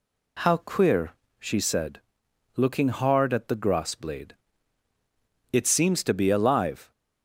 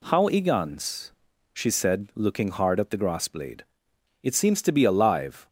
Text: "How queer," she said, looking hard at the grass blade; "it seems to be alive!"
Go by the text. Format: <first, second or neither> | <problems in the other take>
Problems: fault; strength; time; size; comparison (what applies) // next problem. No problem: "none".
first | says "igans" for "queer"; at 0.2 s